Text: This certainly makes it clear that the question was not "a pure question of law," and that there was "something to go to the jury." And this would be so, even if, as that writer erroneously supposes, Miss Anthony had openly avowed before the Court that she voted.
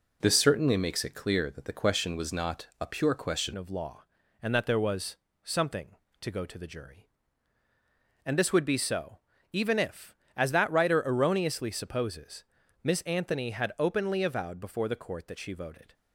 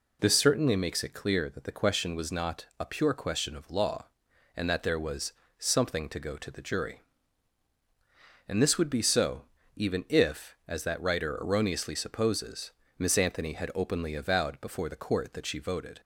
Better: second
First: changes voice at "of"; from 3.5 s on; 12.4 s long // pauses between "was" and "something"; slight; at 5.1 s; 0.28 s long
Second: pauses between "was" and "something"; slight; at 5.3 s; 0.26 s long

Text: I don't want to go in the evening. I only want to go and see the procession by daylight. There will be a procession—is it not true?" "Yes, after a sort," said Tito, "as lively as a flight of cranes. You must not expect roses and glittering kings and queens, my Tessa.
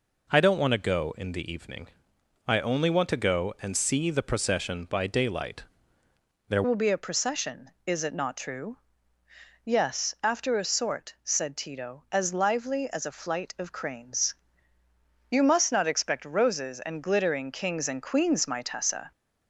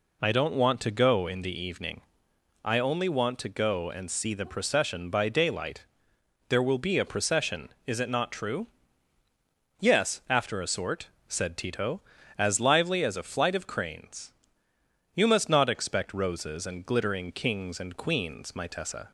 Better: second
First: changes voice at "will"; from 6.6 s on; 12.5 s long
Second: none

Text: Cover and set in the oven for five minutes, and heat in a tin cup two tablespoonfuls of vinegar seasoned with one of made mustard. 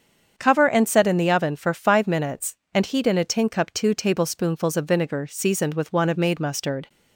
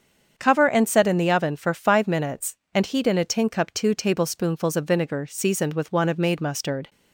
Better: neither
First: starts louder than the rest; strong; until 1.3 s; 7 dB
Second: starts louder than the rest; strong; until 1.3 s; 7 dB

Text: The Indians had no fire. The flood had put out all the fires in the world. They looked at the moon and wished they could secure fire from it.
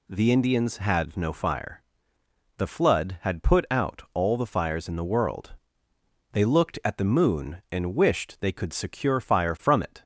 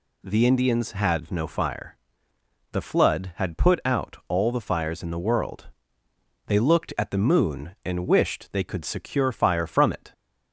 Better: neither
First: none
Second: none

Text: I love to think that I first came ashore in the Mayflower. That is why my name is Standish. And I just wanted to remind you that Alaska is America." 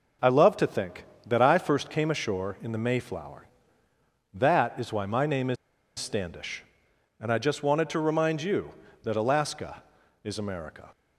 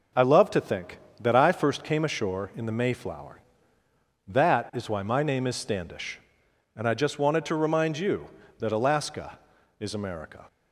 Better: second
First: pauses between "is" and "Standish"; at 5.5 s; 0.43 s long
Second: none

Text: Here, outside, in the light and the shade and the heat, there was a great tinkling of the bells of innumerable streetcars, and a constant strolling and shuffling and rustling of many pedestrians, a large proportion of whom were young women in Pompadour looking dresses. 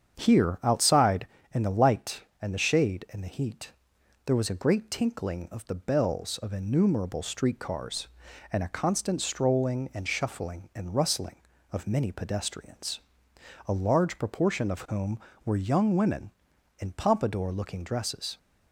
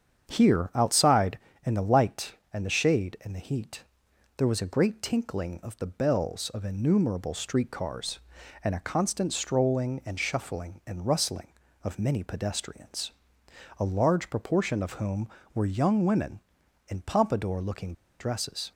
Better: first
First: starts louder than the rest; strong; until 1.2 s; 7.5 dB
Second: starts louder than the rest; strong; until 1.3 s; 7.5 dB // pauses between "looking" and "dresses"; slight; at 17.9 s; 0.27 s long

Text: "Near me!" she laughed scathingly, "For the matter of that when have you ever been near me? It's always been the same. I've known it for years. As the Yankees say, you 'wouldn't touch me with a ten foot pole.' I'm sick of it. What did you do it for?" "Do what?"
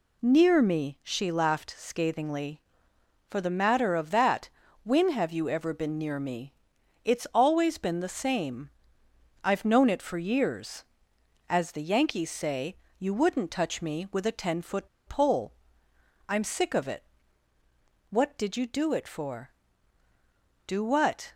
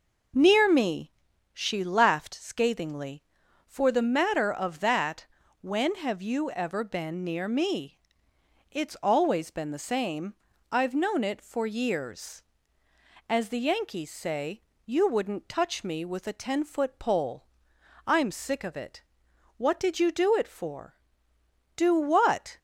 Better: second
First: pauses between "that" and "when"; slight; at 4.4 s; 0.34 s long // pauses between "foot" and "pole"; slight; at 14.8 s; 0.19 s long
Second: pauses between "that" and "when"; slight; at 5.2 s; 0.34 s long

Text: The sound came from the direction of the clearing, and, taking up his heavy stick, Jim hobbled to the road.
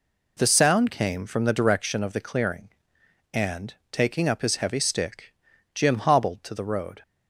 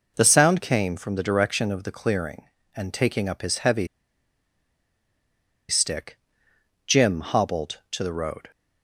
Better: first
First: none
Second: pauses between "heavy" and "stick"; strong; at 3.8 s; 1.8 s long

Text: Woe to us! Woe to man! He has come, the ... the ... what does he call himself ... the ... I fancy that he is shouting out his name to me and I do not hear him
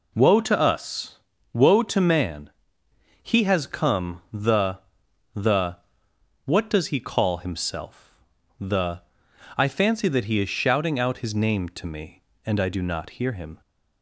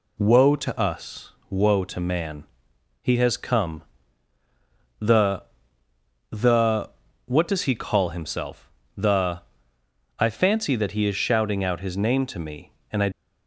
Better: first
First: none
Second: stops before "do not hear him"; at 13.1 s

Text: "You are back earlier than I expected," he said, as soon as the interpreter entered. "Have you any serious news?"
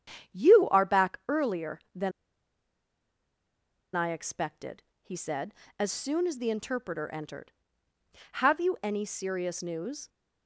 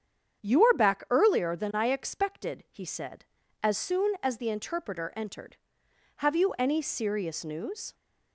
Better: second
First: starts louder than the rest; strong; until 1.4 s; 9 dB // pauses between "than" and "I"; strong; at 2.1 s; 1.8 s long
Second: starts louder than the rest; strong; until 1.4 s; 8 dB

